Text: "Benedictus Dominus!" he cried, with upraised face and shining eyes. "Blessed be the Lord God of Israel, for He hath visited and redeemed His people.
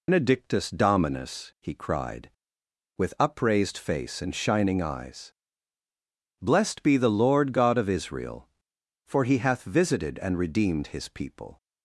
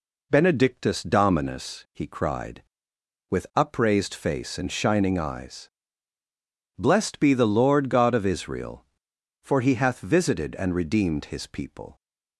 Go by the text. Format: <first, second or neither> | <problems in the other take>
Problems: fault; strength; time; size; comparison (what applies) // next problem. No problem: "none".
second | loses the start of "Benedictus"; at 0.0 s; 115 ms